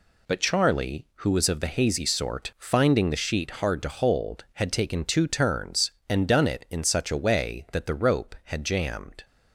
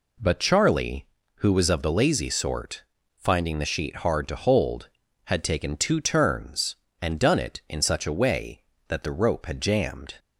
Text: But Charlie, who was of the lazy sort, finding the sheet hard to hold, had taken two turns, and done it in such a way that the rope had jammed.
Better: second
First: says "hazy" for "lazy"; at 1.6 s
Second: none

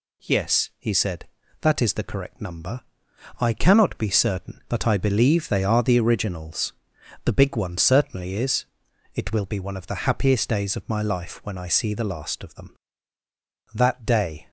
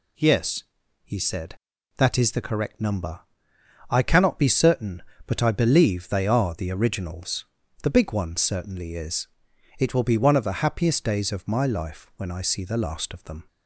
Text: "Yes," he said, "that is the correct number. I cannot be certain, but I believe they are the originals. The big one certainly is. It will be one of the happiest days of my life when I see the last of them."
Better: second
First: goes on to say "That day"; noticeable; from 13.7 s on; 0.76 s long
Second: none

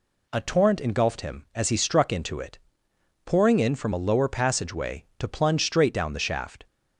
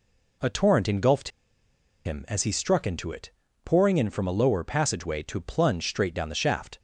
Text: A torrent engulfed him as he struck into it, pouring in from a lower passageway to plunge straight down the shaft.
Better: first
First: none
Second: pauses between "engulfed" and "him"; noticeable; at 1.3 s; 0.75 s long

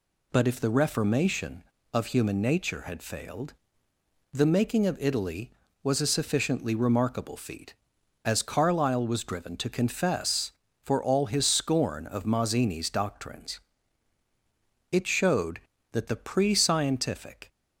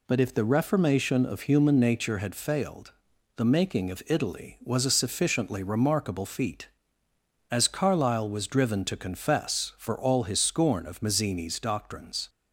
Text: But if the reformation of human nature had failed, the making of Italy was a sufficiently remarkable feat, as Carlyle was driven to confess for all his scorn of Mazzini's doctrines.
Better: second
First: goes on to say "It showed that the pre scientific"; strong; from 14.9 s on; 2.5 s long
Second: none

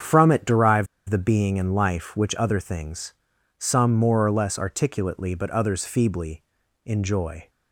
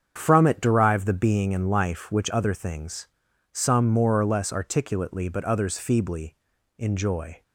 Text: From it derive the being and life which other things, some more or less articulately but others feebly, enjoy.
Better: second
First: starts louder than the rest; strong; until 1.2 s; 7.5 dB // pauses between "derive" and "the"; slight; at 0.8 s; 0.23 s long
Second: starts louder than the rest; strong; until 1.1 s; 7.5 dB

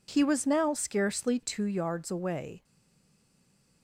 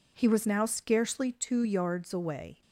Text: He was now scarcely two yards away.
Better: second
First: stays silent after the last word; noticeable; from 2.6 s on; 1.2 s long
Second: none

